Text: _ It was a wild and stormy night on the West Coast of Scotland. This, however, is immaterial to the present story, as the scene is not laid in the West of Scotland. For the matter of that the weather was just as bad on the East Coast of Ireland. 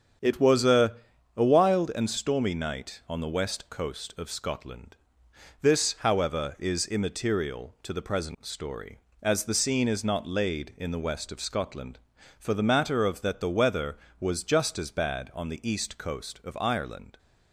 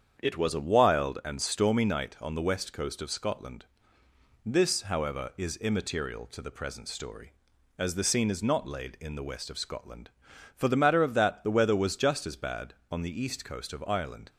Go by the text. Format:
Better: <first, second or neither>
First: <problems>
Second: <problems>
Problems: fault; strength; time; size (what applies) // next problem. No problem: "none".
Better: second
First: starts louder than the rest; strong; until 1.6 s; 8 dB // says "a" twice; at 1.3 s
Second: starts louder than the rest; strong; until 1.2 s; 8 dB